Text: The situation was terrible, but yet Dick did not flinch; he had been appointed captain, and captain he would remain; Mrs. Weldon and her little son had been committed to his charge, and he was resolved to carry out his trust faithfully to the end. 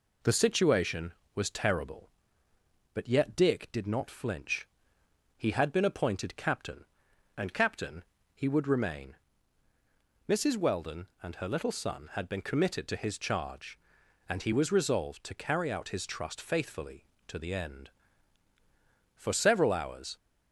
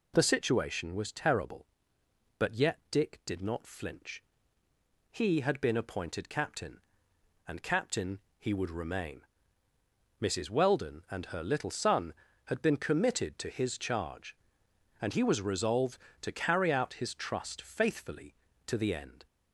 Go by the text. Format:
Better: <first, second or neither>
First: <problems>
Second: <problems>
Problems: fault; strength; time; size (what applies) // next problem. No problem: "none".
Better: second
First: pauses between "captain" and "he"; slight; at 8.0 s; 0.32 s long // goes on to say "For several hours"; noticeable; from 19.1 s on; 1.0 s long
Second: pauses between "captain" and "he"; slight; at 8.2 s; 0.17 s long